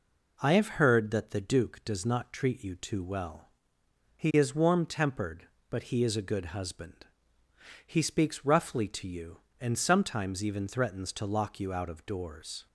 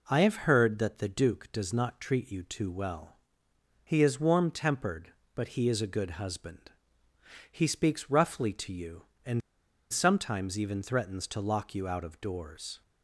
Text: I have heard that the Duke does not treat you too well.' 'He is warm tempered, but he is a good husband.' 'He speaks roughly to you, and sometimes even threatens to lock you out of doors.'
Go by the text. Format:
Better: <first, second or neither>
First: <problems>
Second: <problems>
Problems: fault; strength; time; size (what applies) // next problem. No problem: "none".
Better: first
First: none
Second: pauses between "and" and "sometimes"; noticeable; at 9.4 s; 0.50 s long